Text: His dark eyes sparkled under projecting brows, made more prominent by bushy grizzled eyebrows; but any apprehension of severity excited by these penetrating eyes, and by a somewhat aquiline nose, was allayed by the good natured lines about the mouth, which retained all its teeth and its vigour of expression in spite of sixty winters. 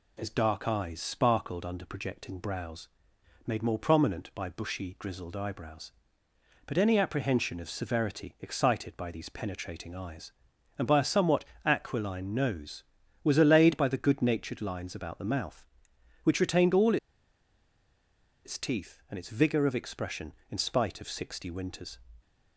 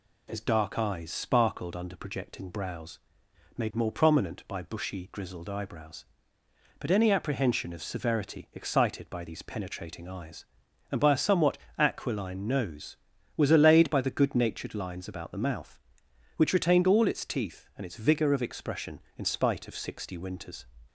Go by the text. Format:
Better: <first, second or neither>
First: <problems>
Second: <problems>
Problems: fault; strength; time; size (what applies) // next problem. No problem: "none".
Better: second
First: pauses between "somewhat" and "aquiline"; slight; at 11.4 s; 0.20 s long // pauses between "all" and "its"; strong; at 16.9 s; 1.4 s long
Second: pauses between "somewhat" and "aquiline"; slight; at 11.5 s; 0.20 s long